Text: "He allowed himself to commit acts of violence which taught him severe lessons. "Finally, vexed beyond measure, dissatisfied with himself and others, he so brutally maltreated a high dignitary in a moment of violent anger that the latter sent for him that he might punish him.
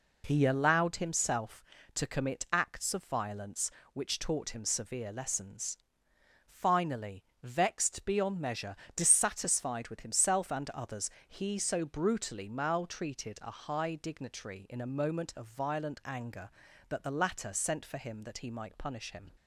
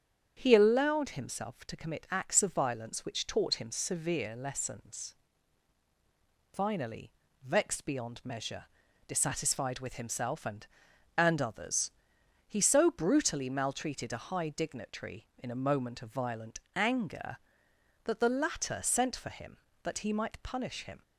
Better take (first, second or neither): first